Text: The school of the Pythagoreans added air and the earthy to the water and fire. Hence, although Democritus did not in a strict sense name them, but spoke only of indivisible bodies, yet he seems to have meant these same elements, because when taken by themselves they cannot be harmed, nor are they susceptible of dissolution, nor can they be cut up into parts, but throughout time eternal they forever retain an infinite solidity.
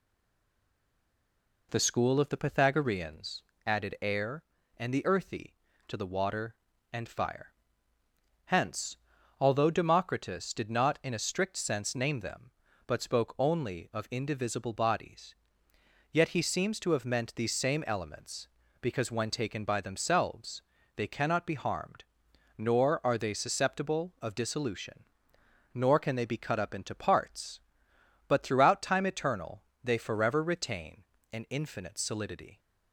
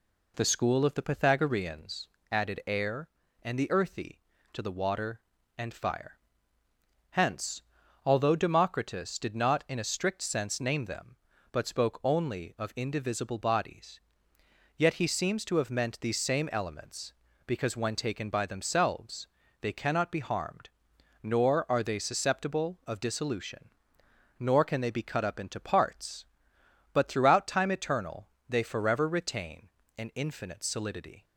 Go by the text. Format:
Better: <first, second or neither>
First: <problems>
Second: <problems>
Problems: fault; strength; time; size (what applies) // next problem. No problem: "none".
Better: second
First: stays silent before the first word; noticeable; until 1.7 s; 1.7 s long // pauses between "Pythagoreans" and "added"; slight; at 3.4 s; 0.24 s long // pauses between "themselves" and "they"; slight; at 20.6 s; 0.32 s long // pauses between "eternal" and "they"; slight; at 29.6 s; 0.22 s long // pauses between "retain" and "an"; slight; at 31.0 s; 0.28 s long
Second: pauses between "Pythagoreans" and "added"; slight; at 2.0 s; 0.24 s long // pauses between "themselves" and "they"; slight; at 19.2 s; 0.32 s long // pauses between "eternal" and "they"; slight; at 28.2 s; 0.22 s long // pauses between "retain" and "an"; slight; at 29.6 s; 0.28 s long